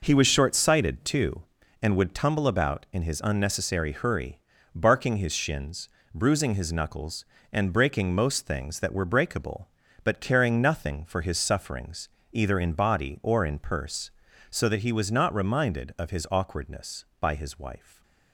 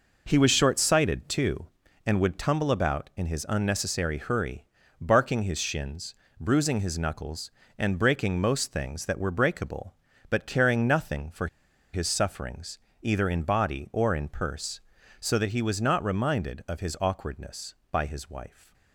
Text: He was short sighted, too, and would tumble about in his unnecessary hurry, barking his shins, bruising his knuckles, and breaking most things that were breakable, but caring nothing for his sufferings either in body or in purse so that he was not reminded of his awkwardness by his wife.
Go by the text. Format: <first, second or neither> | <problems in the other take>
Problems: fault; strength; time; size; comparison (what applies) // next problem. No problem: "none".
first | pauses between "for" and "his"; noticeable; at 11.4 s; 0.46 s long // pauses between "sufferings" and "either"; slight; at 12.7 s; 0.22 s long; slight in the first